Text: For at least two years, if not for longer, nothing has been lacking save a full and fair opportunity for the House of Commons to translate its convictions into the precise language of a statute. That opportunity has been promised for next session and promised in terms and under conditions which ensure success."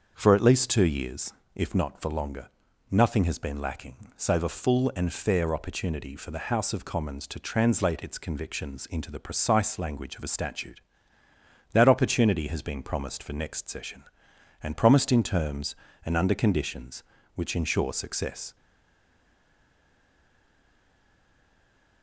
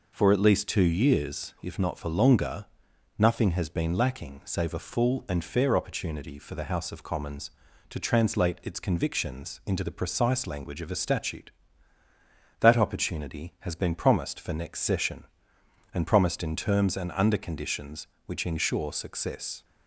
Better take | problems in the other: second | starts louder than the rest; until 1.1 s; 6.5 dB // pauses between "lacking" and "save"; slight; at 3.9 s; 0.20 s long // stays silent after the last word; strong; from 18.5 s on; 3.5 s long

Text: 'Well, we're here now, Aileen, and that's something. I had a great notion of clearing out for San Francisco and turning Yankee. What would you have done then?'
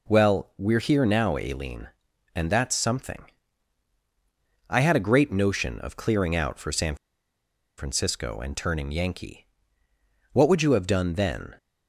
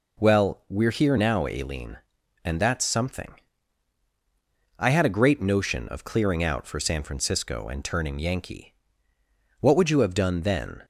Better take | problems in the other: second | pauses between "San" and "Francisco"; noticeable; at 6.9 s; 0.82 s long

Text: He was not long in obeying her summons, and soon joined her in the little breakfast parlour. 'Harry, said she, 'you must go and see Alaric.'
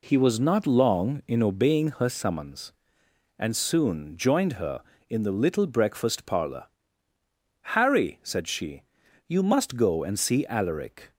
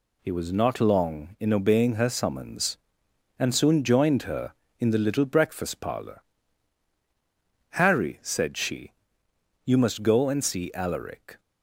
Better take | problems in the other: neither | none

